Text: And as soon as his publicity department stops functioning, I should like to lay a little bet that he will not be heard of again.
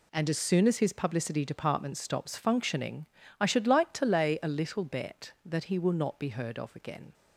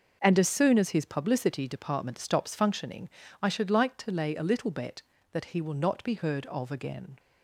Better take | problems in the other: neither | none

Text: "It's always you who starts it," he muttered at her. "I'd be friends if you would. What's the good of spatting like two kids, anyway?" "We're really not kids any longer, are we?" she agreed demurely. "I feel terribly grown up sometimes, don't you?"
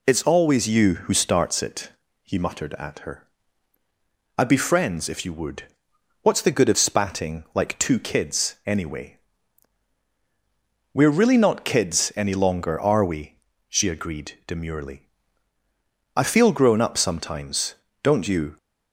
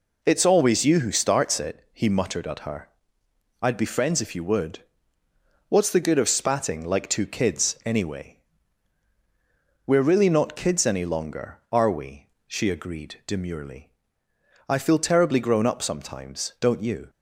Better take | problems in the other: second | skips "terribly"; at 16.5 s

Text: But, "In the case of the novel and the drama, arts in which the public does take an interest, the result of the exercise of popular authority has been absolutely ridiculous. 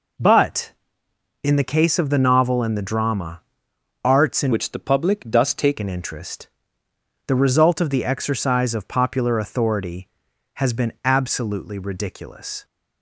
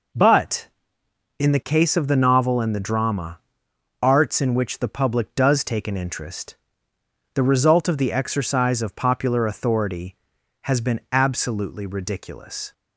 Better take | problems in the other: second | changes voice from "which" to "take"; from 4.5 to 5.7 s; 1.2 s long

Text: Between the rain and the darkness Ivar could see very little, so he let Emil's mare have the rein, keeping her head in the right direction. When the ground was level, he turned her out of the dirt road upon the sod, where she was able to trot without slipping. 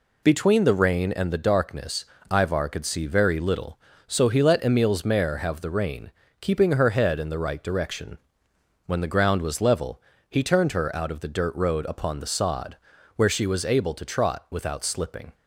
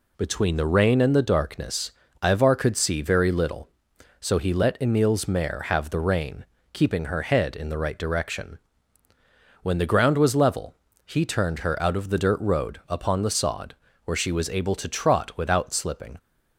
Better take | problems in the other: neither | pauses between "darkness" and "Ivar"; slight; the same in both

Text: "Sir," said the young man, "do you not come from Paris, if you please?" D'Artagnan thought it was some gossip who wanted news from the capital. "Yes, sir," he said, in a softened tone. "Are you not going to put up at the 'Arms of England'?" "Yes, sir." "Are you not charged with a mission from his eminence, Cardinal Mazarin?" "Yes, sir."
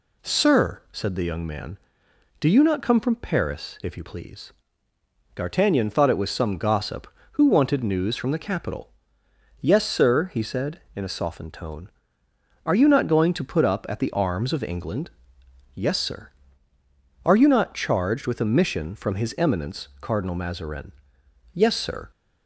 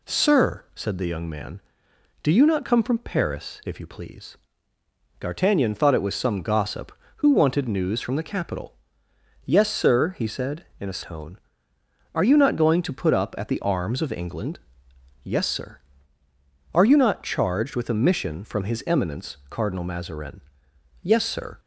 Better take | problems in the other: first | skips "softened"; at 11.0 s

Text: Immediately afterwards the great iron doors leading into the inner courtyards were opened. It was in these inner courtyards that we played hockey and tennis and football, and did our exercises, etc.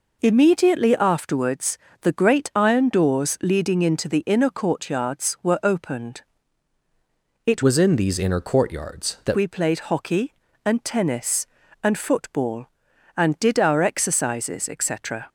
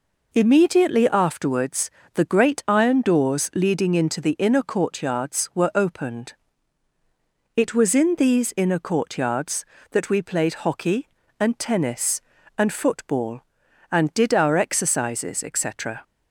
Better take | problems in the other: second | pauses between "afterwards" and "the"; slight; at 1.7 s; 0.24 s long; slight in the second // changes voice from "was" to "that"; from 7.6 to 9.3 s; 1.7 s long

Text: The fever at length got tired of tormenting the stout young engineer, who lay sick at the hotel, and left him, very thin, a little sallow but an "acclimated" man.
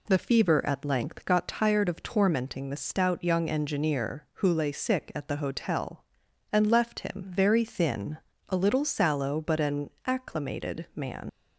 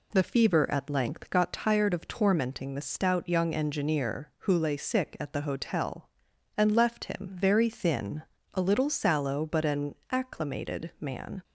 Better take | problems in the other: second | pauses between "an" and "acclimated"; slight; at 9.9 s; 0.16 s long; slight in the second // leaves "man" unfinished; at 11.2 s; 85 ms

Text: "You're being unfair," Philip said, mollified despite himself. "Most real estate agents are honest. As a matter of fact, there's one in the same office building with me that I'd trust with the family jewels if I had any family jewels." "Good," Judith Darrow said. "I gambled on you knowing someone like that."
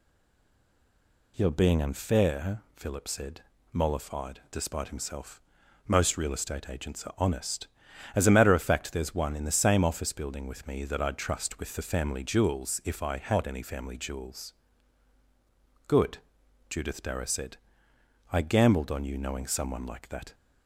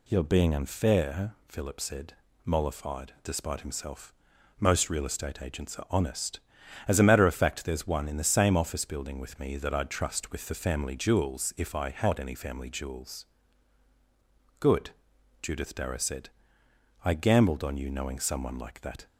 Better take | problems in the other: second | stays silent before the first word; noticeable; until 1.3 s; 1.3 s long

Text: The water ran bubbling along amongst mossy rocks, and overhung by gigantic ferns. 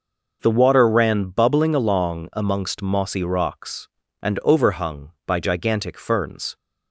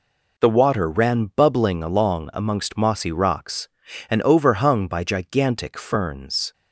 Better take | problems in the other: neither | none

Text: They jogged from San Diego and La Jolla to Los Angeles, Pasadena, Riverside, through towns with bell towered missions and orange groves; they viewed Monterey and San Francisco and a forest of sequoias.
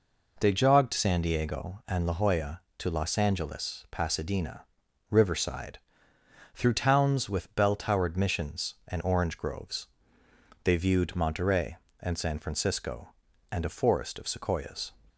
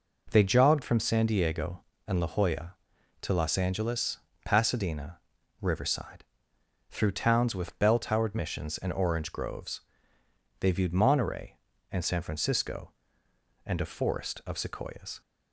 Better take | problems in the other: second | skips "from"; at 0.9 s

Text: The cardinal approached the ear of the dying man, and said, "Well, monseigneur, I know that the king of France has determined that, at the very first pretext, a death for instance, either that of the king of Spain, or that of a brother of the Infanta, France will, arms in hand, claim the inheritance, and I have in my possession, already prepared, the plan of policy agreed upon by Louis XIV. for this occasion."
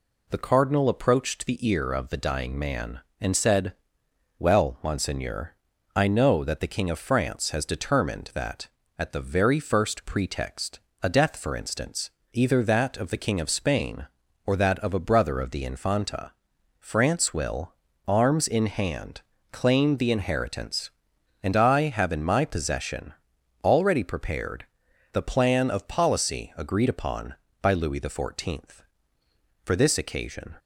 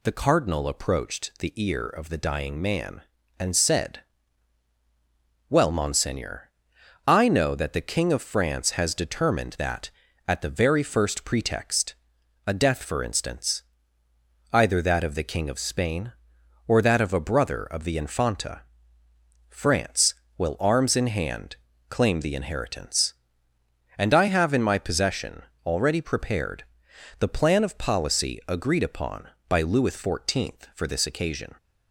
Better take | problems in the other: neither | none

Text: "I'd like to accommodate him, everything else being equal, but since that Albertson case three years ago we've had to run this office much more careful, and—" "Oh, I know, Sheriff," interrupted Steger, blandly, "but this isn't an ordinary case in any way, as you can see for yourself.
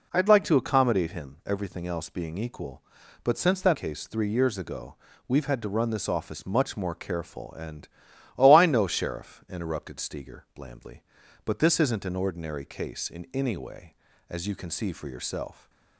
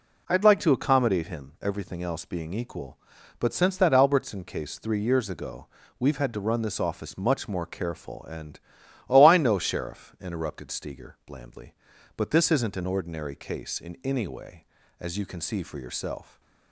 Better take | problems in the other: second | skips "Albertson"; at 3.7 s // pauses between "ago" and "we've"; slight; at 4.9 s; 0.32 s long; slight in the second

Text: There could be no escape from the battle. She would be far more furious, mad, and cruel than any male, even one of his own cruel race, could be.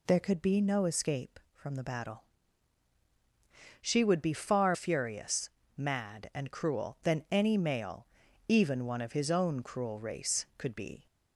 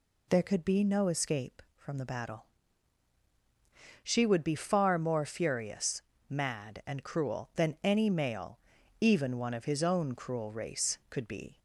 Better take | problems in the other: second | skips "more"; at 4.7 s

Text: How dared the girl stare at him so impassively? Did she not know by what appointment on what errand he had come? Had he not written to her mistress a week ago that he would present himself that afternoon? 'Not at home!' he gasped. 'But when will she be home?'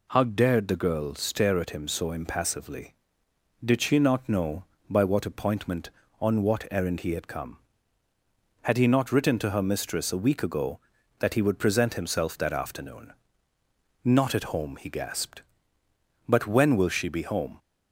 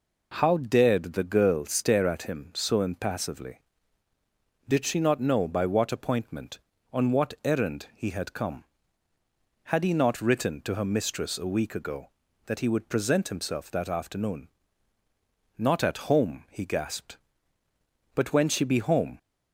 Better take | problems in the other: first | skips "will"; at 18.4 s

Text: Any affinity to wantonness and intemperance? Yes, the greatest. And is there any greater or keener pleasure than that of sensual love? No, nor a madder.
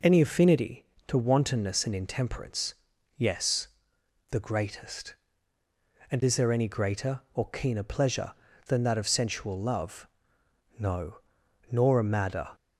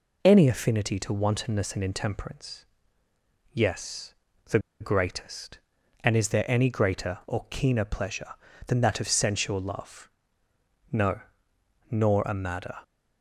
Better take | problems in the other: first | pauses between "the" and "greatest"; slight; at 4.5 s; 0.22 s long

